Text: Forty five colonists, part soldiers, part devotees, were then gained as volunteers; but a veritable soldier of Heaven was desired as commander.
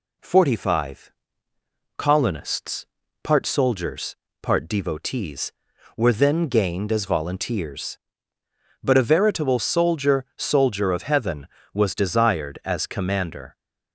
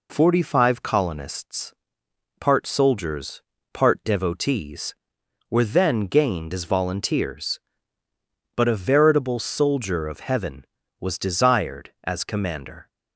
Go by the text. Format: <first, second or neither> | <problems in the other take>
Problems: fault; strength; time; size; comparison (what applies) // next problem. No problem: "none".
second | pauses between "five" and "colonists"; noticeable; at 1.1 s; 0.86 s long // says "soldier" twice; at 10.3 s